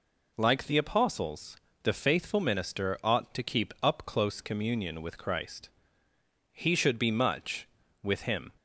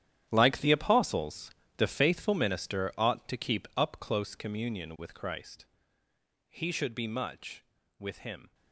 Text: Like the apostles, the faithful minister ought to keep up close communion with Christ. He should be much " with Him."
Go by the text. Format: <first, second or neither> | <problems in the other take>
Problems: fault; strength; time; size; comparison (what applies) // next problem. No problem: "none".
first | gets quieter; strong; throughout; 19 dB